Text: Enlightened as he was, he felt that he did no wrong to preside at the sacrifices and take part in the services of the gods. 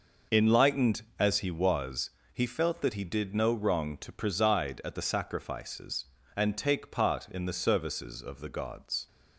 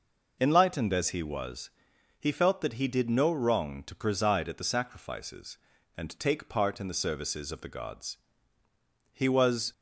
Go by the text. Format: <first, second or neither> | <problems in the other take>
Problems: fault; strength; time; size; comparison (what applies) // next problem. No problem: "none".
first | goes on to say "He was"; from 9.1 s on; 0.60 s long